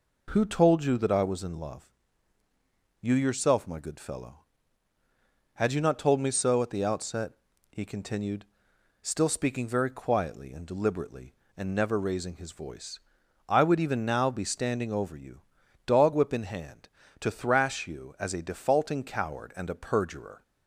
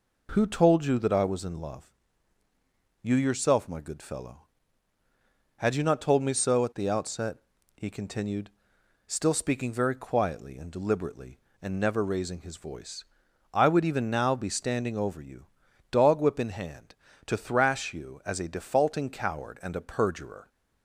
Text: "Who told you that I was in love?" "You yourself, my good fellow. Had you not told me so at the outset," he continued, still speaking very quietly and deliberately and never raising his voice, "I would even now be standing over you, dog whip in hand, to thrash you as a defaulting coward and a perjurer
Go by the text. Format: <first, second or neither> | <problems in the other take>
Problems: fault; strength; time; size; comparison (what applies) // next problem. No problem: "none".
neither | none